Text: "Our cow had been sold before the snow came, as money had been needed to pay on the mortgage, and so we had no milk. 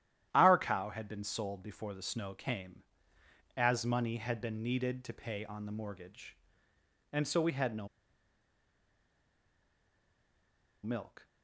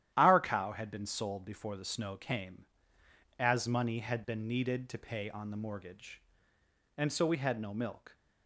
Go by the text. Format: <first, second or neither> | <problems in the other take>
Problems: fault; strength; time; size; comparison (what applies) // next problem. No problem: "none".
second | starts louder than the rest; strong; until 1.3 s; 11.5 dB; strong in the second // pauses between "no" and "milk"; strong; at 7.8 s; 2.9 s long